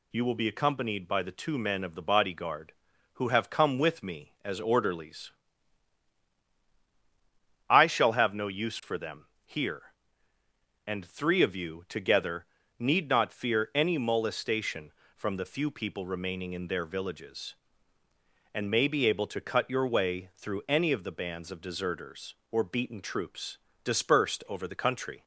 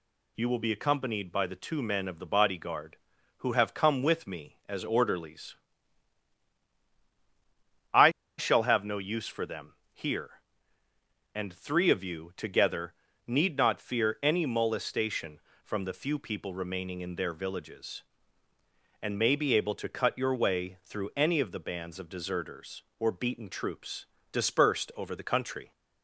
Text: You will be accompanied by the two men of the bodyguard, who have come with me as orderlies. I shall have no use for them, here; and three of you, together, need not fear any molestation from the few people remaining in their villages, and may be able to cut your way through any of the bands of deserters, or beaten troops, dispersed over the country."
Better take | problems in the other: first | pauses between "I" and "shall"; slight; at 8.1 s; 0.27 s long

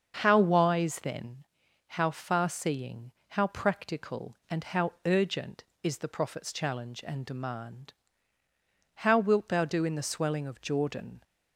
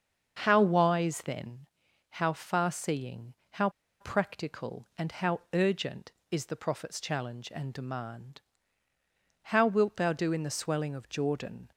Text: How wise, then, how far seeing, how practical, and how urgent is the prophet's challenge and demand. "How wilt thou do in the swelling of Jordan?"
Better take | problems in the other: first | starts louder than the rest; until 1.4 s; 6.5 dB; also in the first // pauses between "how" and "practical"; slight; at 3.6 s; 0.31 s long

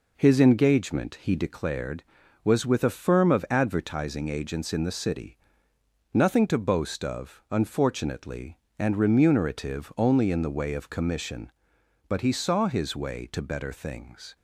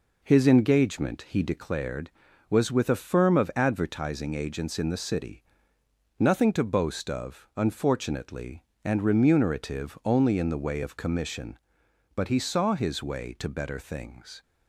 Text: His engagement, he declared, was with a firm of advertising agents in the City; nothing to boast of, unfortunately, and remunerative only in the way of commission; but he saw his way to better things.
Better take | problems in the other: neither | none

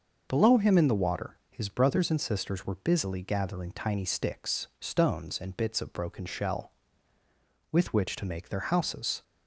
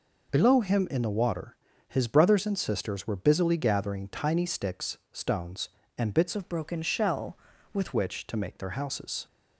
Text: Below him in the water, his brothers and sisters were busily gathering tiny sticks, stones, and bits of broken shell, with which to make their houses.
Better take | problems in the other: first | changes voice from "of" to "with"; from 6.3 to 7.9 s; 1.6 s long

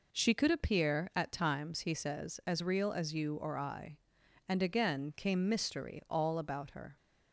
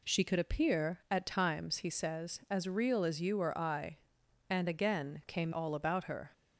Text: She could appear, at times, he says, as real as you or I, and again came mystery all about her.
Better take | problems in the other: first | skips "mystery"; at 5.5 s

